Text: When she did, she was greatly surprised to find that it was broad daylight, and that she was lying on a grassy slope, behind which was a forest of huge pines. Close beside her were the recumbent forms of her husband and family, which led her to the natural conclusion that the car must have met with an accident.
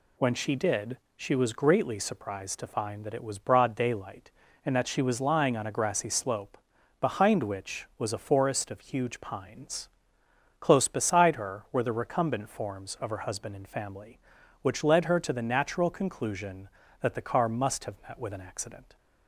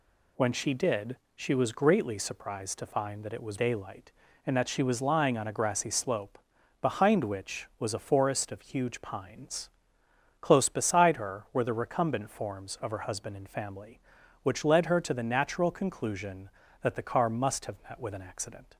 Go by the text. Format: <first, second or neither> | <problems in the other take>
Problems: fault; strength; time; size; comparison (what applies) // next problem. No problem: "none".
first | skips "broad"; at 3.5 s